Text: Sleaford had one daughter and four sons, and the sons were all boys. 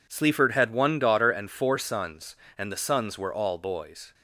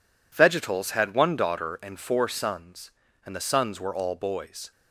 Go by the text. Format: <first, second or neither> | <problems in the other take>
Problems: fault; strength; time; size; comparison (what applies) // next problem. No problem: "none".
first | says "Vegetals" for "Sleaford"; at 0.3 s